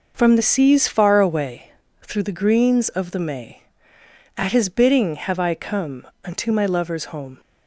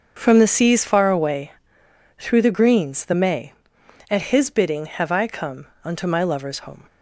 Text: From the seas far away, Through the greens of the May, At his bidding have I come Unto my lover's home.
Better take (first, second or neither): first